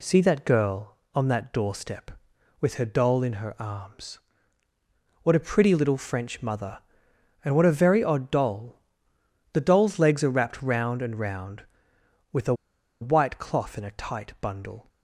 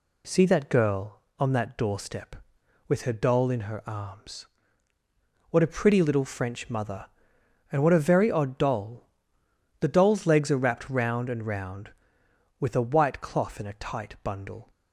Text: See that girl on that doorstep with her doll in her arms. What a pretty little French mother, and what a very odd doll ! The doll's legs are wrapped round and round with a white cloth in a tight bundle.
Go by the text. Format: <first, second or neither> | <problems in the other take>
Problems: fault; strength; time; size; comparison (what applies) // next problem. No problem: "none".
second | pauses between "a" and "white"; noticeable; at 12.5 s; 0.47 s long